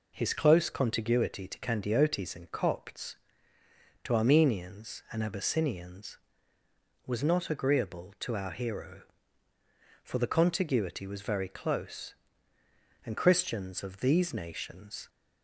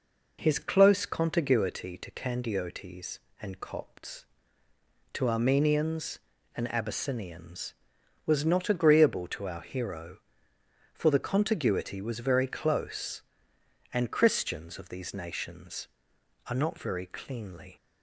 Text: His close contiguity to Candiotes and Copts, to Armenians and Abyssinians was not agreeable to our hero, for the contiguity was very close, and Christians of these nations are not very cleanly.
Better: second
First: stops before "are not very cleanly"; at 15.0 s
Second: none

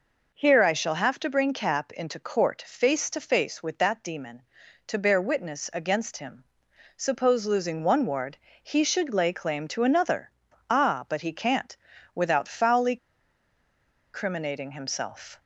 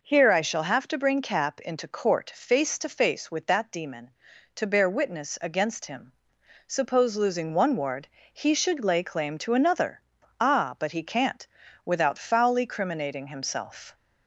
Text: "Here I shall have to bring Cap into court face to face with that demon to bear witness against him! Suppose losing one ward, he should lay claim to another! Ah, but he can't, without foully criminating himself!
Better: second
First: pauses between "foully" and "criminating"; at 12.9 s; 1.1 s long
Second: none

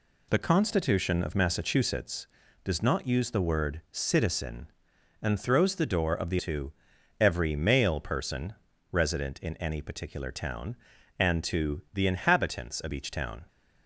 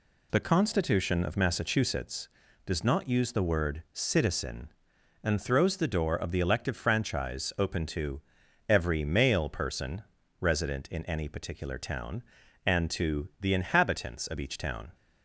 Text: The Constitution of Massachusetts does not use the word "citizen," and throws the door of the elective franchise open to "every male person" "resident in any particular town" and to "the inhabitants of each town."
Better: second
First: skips "elective franchise open"; at 6.3 s // pauses between "to" and "every"; noticeable; at 6.7 s; 0.48 s long // pauses between "person" and "resident"; slight; at 8.5 s; 0.36 s long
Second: pauses between "to" and "every"; noticeable; at 8.2 s; 0.48 s long // pauses between "person" and "resident"; slight; at 10.0 s; 0.36 s long

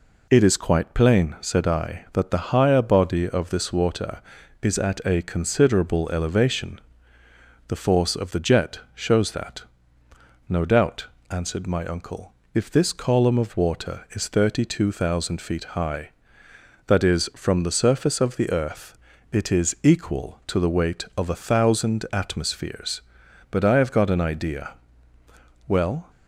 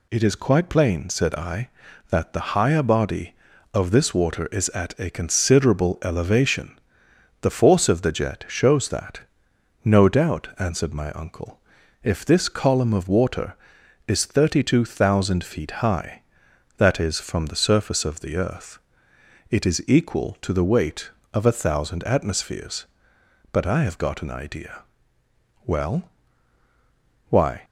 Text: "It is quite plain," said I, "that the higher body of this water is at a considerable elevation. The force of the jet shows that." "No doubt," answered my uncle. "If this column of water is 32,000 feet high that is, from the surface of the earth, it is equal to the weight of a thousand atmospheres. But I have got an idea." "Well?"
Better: first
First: none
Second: goes on to say "Why"; slight; from 27.2 s on; 0.34 s long

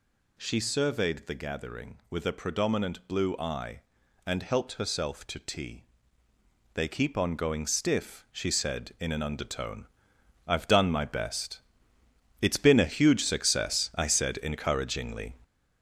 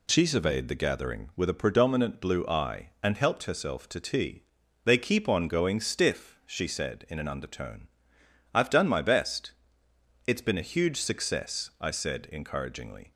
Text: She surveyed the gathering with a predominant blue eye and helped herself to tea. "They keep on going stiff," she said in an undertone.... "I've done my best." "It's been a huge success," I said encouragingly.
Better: second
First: gets louder; throughout; 6.5 dB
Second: none

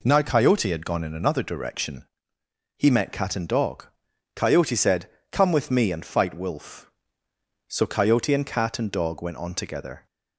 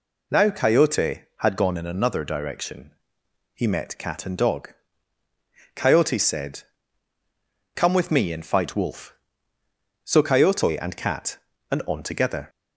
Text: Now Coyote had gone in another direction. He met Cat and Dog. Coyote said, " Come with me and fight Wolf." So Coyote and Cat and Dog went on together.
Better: first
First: none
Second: skips "Dog went"; at 11.8 s

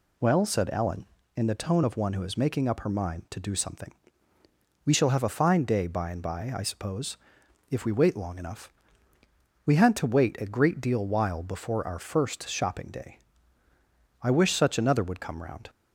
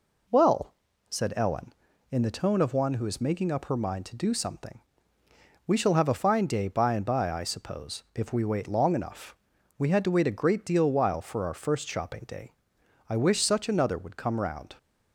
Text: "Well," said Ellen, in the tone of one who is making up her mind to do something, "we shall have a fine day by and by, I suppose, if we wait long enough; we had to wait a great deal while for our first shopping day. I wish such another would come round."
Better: second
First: says "before" for "for"; at 11.4 s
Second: none

